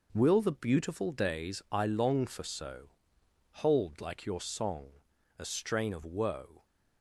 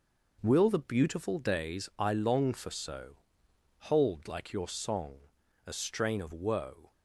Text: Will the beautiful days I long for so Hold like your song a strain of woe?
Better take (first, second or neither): neither